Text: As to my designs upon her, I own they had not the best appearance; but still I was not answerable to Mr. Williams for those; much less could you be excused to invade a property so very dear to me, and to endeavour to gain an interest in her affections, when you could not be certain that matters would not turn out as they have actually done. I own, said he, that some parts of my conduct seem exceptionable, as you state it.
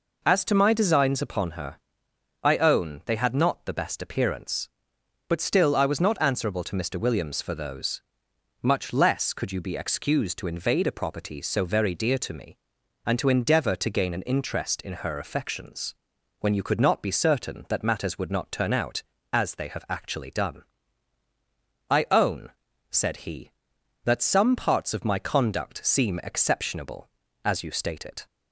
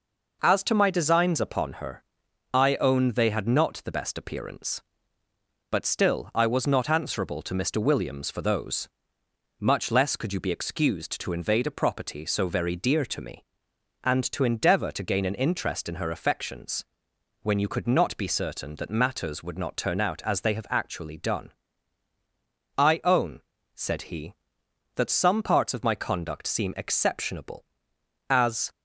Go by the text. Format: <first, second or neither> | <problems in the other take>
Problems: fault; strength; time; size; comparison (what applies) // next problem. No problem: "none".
first | stops before "you state it"; at 28.7 s